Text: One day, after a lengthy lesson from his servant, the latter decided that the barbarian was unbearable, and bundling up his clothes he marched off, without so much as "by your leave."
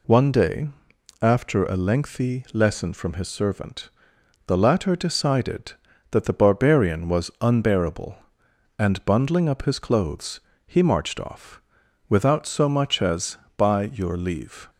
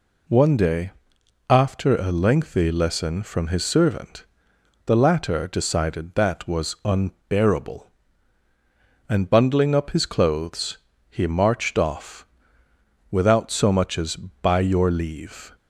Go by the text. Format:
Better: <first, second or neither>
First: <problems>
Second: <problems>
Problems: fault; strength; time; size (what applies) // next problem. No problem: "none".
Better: first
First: pauses between "clothes" and "he"; slight; at 10.3 s; 0.28 s long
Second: skips "the barbarian"; at 6.4 s // pauses between "clothes" and "he"; slight; at 10.7 s; 0.30 s long